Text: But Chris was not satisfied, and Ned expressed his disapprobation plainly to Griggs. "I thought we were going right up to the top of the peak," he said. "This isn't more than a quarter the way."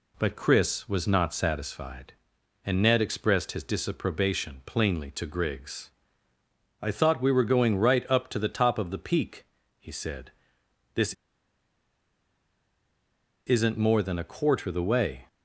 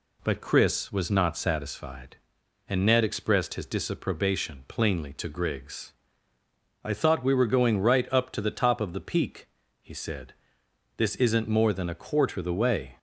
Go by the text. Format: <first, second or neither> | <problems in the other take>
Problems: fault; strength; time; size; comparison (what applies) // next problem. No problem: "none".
second | pauses between "This" and "isn't"; strong; at 11.1 s; 2.3 s long